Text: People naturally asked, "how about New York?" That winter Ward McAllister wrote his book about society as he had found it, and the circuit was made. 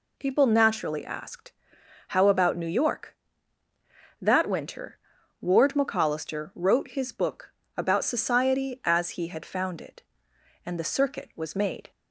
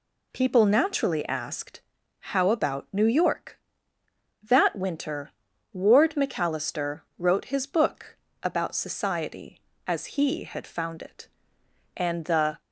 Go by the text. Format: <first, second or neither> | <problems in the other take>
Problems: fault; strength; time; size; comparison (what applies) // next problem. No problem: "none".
first | pauses between "winter" and "Ward"; at 5.3 s; 0.40 s long; noticeable in the first // pauses between "McAllister" and "wrote"; slight; at 7.0 s; 0.18 s long // pauses between "book" and "about"; slight; at 8.1 s; 0.26 s long; slight in the first // stops before "circuit was made"; at 12.6 s